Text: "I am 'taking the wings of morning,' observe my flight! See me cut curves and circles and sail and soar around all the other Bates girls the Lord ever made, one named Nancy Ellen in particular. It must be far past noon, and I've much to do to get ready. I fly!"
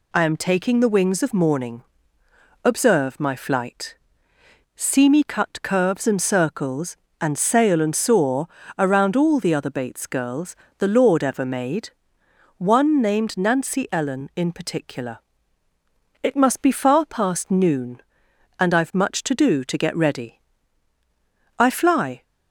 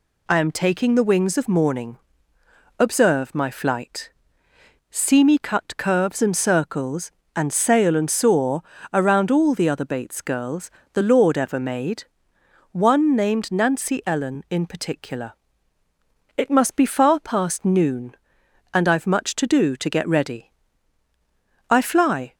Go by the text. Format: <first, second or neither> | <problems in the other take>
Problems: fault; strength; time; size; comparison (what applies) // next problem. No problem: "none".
neither | pauses between "soar" and "around"; slight; the same in both // pauses between "girls" and "the"; slight; the same in both